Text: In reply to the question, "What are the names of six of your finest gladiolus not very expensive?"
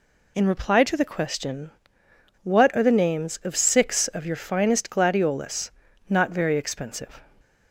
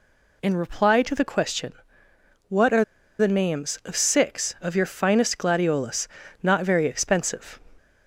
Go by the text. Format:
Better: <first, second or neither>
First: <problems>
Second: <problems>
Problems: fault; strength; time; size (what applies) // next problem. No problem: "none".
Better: first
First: pauses between "gladiolus" and "not"; at 5.7 s; 0.38 s long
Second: pauses between "are" and "the"; slight; at 2.8 s; 0.35 s long // pauses between "gladiolus" and "not"; slight; at 6.0 s; 0.34 s long